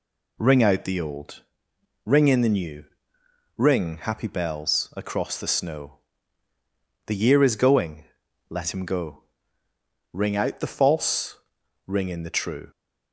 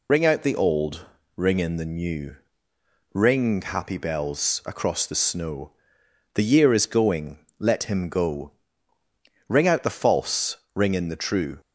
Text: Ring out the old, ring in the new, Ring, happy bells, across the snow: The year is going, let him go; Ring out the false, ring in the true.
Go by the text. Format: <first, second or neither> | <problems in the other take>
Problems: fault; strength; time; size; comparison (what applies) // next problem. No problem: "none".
first | loses the start of "Ring"; at 0.0 s; 60 ms